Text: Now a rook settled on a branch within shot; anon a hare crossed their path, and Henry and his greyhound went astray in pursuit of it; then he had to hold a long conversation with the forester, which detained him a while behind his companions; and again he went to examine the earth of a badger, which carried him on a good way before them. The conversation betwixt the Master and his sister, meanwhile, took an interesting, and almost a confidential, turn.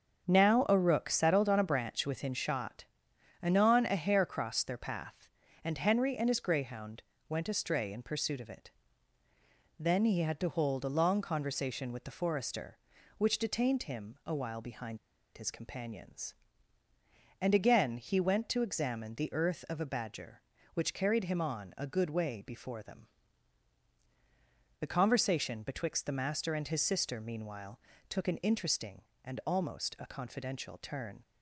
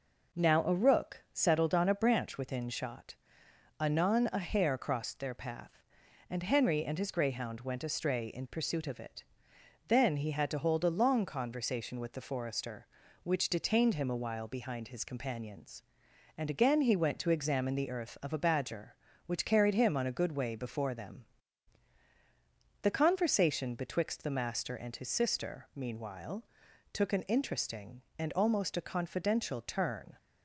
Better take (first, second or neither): second